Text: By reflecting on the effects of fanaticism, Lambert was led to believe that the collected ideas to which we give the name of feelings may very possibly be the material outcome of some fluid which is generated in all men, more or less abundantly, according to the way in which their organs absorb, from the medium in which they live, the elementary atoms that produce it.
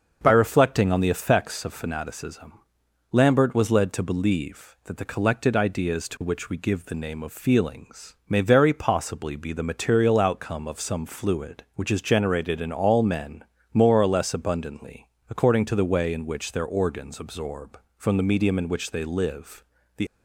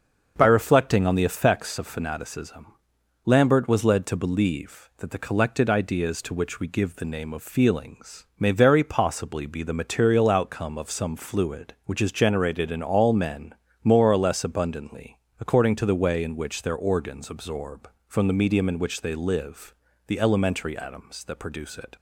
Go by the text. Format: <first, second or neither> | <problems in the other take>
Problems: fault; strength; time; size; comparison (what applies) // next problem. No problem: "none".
second | stops before "elementary atoms that produce it"; at 20.0 s